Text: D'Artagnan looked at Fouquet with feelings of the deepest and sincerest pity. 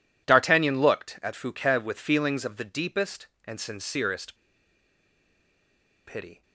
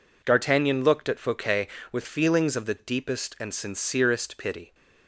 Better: second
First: pauses between "sincerest" and "pity"; strong; at 4.3 s; 1.7 s long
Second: none

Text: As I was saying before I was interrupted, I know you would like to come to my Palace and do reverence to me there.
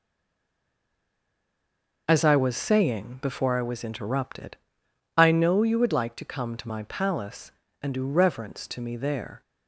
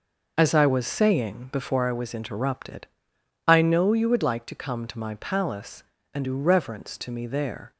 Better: second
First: stays silent before the first word; noticeable; until 2.0 s; 2.0 s long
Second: none

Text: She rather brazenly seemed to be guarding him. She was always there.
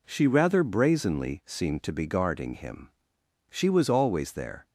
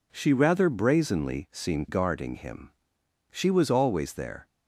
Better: first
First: none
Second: skips "to be"; at 1.8 s

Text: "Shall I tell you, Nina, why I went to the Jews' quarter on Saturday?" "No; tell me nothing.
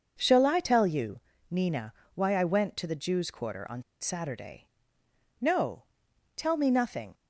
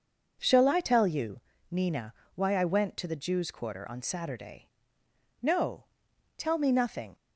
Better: second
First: pauses between "on" and "Saturday"; slight; at 3.8 s; 0.18 s long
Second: none

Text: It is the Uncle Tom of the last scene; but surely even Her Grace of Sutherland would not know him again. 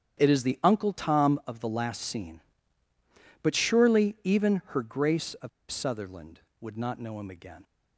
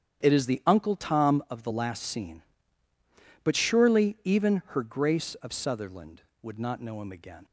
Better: second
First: starts louder than the rest; strong; until 1.2 s; 9 dB // pauses between "of" and "Sutherland"; slight; at 5.4 s; 0.21 s long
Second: starts louder than the rest; strong; until 1.2 s; 9 dB

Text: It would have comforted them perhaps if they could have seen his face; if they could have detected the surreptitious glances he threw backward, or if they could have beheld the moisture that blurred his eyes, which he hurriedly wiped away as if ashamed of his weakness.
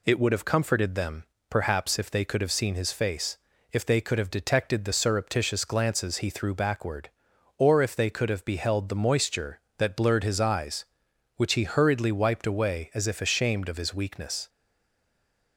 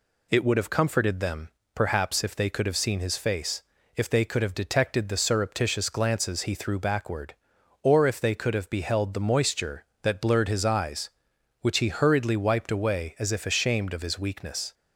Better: second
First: pauses between "them" and "perhaps"; slight; at 1.2 s; 0.26 s long // stays silent after the last word; from 14.4 s on; 1.1 s long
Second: pauses between "them" and "perhaps"; slight; at 1.4 s; 0.26 s long

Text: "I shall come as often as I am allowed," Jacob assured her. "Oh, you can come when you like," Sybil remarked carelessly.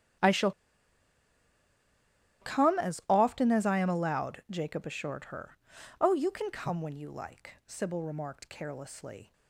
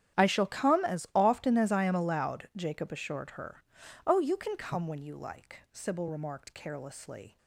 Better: second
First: starts louder than the rest; strong; until 3.2 s; 10 dB // pauses between "shall" and "come"; strong; at 0.5 s; 1.9 s long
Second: starts louder than the rest; strong; until 1.2 s; 10 dB

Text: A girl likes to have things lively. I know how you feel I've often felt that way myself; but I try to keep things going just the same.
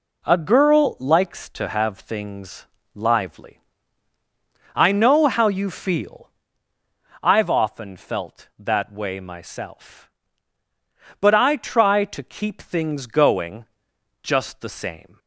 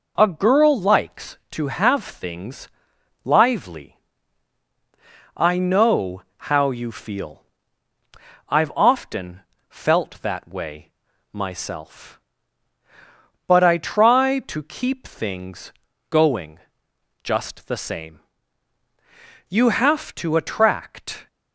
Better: first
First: pauses between "things" and "lively"; slight; at 2.6 s; 0.28 s long // pauses between "feel" and "I've"; noticeable; at 6.3 s; 0.94 s long // pauses between "going" and "just"; noticeable; at 13.6 s; 0.58 s long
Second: pauses between "things" and "lively"; noticeable; at 2.6 s; 0.56 s long // pauses between "know" and "how"; slight; at 6.2 s; 0.26 s long // pauses between "feel" and "I've"; at 7.4 s; 1.0 s long // pauses between "often" and "felt"; slight; at 9.4 s; 0.26 s long // pauses between "way" and "myself"; at 10.9 s; 0.42 s long // pauses between "things" and "going"; slight; at 15.7 s; 0.36 s long // pauses between "going" and "just"; noticeable; at 16.5 s; 0.62 s long // goes on to say "You have to attract"; strong; from 19.4 s on; 1.7 s long

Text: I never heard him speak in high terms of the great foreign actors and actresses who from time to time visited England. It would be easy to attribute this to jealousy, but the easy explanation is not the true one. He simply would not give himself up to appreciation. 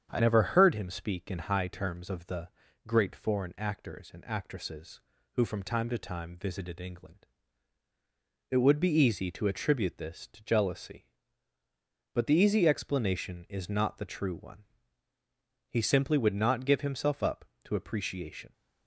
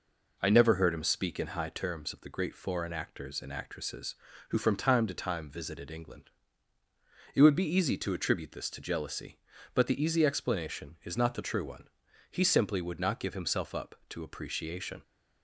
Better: second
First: starts louder than the rest; strong; until 1.1 s; 8 dB // changes voice at "never"; from 0.1 s on; 18.4 s long // pauses between "the" and "great"; at 2.4 s; 0.38 s long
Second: none

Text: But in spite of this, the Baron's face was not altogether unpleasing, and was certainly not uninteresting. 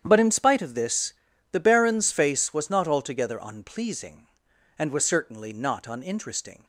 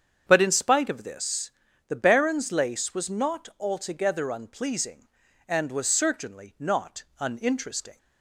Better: first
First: starts louder than the rest; strong; until 1.0 s; 9 dB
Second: starts louder than the rest; strong; until 1.2 s; 7.5 dB // says "lace" for "face"; at 2.5 s

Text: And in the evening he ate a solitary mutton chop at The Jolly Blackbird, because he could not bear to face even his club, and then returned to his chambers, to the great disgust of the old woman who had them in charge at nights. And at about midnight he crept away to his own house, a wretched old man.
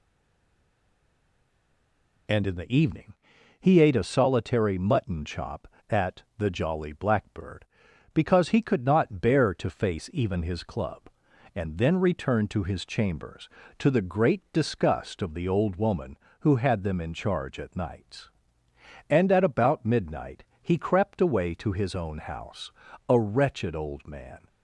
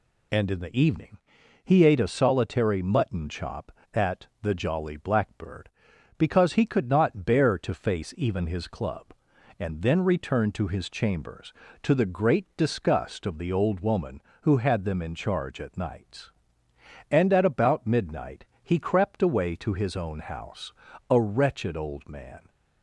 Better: second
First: stays silent before the first word; until 2.2 s; 2.2 s long // pauses between "evening" and "he"; noticeable; at 3.1 s; 0.46 s long // pauses between "at" and "The"; slight; at 6.2 s; 0.16 s long // pauses between "midnight" and "he"; slight; at 20.4 s; 0.18 s long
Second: pauses between "evening" and "he"; noticeable; at 1.1 s; 0.46 s long // pauses between "at" and "The"; slight; at 4.2 s; 0.16 s long // pauses between "midnight" and "he"; slight; at 18.4 s; 0.18 s long

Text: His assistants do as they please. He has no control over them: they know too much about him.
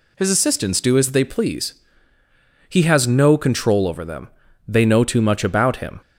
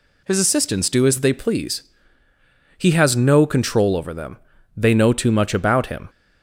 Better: neither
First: none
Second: none

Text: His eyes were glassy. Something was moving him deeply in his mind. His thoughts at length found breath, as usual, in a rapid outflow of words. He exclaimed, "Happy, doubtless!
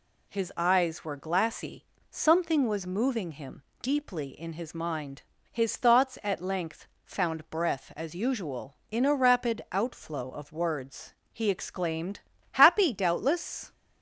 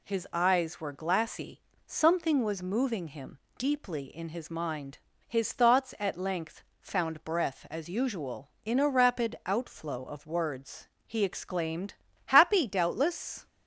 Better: neither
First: pauses between "him" and "deeply"; slight; at 3.6 s; 0.18 s long // pauses between "length" and "found"; slight; at 6.8 s; 0.18 s long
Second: pauses between "him" and "deeply"; slight; at 3.3 s; 0.18 s long // pauses between "length" and "found"; slight; at 6.6 s; 0.18 s long

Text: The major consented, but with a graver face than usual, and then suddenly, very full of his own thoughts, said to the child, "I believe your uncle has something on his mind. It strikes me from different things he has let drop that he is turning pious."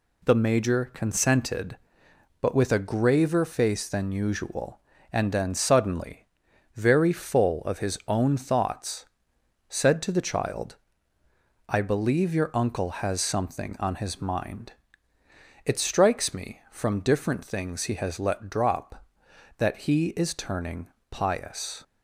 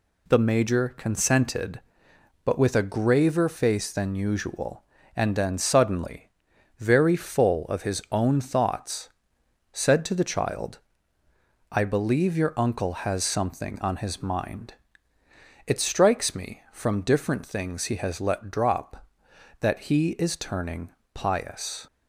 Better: neither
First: pauses between "turning" and "pious"; slight; at 20.8 s; 0.21 s long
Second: pauses between "turning" and "pious"; slight; at 20.9 s; 0.22 s long

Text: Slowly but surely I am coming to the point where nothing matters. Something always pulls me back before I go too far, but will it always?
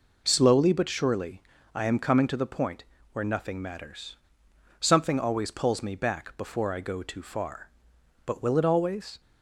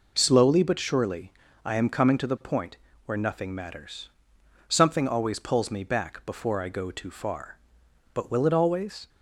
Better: neither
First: pauses between "surely" and "I"; slight; at 1.4 s; 0.34 s long // pauses between "point" and "where"; slight; at 2.8 s; 0.26 s long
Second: pauses between "surely" and "I"; slight; at 1.3 s; 0.34 s long // pauses between "point" and "where"; slight; at 2.7 s; 0.26 s long

